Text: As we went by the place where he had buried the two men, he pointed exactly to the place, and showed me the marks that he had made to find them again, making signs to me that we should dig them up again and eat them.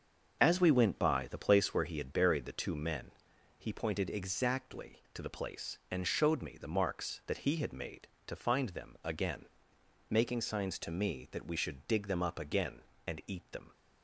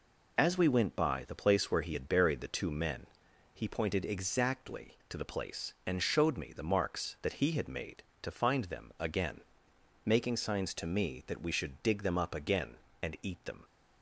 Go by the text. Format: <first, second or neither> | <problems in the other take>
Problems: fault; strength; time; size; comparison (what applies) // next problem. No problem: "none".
second | starts louder than the rest; until 1.8 s; 6.5 dB